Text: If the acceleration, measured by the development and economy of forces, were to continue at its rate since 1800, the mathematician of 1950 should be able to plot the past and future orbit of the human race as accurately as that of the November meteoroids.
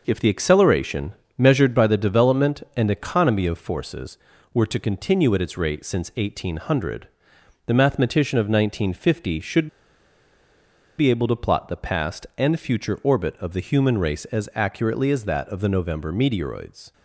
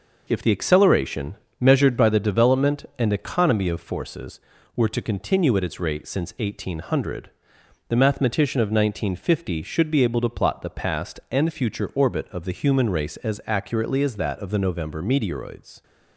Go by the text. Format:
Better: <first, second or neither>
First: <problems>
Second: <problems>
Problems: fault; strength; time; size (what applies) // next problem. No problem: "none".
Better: second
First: pauses between "should" and "be"; strong; at 9.6 s; 1.3 s long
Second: none